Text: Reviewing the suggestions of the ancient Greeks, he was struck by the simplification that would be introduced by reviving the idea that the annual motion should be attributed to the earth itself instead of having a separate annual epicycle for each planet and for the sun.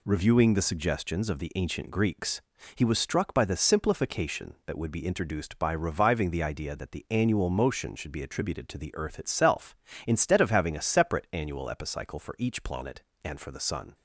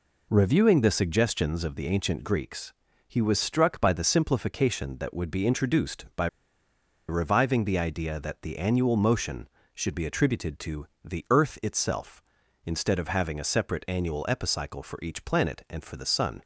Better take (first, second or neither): first